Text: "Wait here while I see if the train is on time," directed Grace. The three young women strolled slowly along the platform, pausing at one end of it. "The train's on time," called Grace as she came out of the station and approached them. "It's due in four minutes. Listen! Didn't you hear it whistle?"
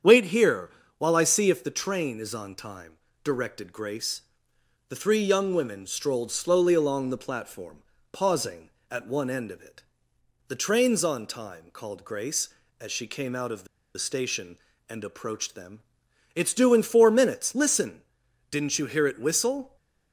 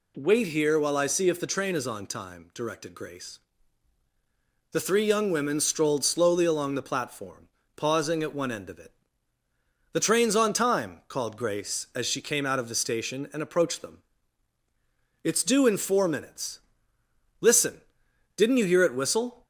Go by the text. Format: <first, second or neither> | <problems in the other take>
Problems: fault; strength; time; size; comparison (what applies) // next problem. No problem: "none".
second | starts louder than the rest; strong; until 1.3 s; 8 dB // pauses between "here" and "while"; slight; at 0.6 s; 0.30 s long // pauses between "the" and "station"; slight; at 13.6 s; 0.30 s long